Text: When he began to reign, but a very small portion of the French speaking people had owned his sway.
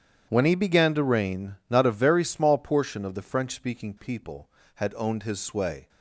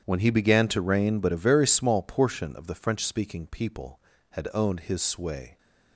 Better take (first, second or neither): second